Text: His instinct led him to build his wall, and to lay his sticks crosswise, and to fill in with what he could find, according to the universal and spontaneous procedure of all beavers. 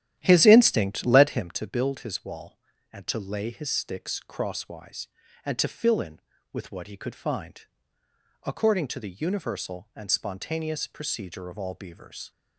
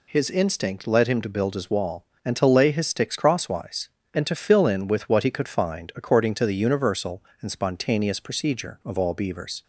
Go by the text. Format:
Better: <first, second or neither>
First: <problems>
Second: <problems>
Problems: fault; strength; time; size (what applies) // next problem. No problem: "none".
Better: second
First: starts louder than the rest; strong; until 1.6 s; 11.5 dB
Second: none